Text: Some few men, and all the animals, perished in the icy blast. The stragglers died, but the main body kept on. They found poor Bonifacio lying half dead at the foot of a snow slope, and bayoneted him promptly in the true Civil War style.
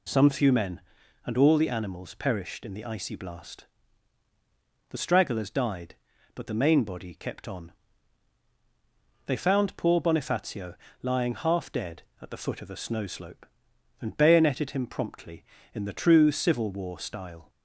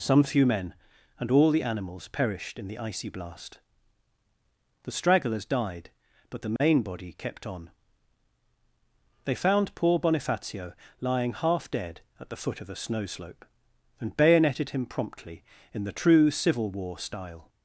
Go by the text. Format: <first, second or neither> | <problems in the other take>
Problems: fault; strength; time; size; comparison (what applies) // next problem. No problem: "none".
neither | pauses between "Bonifacio" and "lying"; slight; the same in both